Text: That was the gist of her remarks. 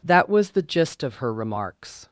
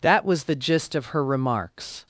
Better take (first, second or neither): neither